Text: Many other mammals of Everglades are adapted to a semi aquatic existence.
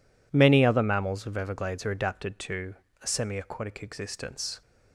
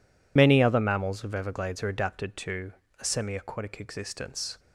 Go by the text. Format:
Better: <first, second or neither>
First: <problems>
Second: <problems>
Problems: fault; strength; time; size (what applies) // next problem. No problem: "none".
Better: first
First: pauses between "to" and "a"; slight; at 2.7 s; 0.26 s long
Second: loses the start of "Many"; at 0.3 s; 70 ms // pauses between "to" and "a"; slight; at 2.7 s; 0.26 s long